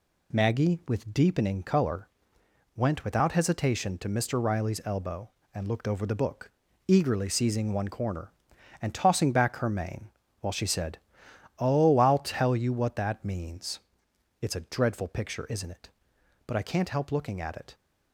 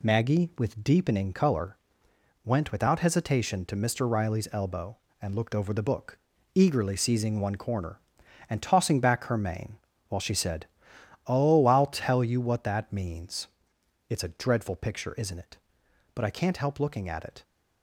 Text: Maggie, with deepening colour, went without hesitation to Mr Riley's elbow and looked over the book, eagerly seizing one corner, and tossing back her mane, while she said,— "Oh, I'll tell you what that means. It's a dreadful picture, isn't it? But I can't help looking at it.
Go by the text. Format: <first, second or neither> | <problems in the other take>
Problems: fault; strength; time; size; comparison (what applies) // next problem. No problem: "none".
neither | none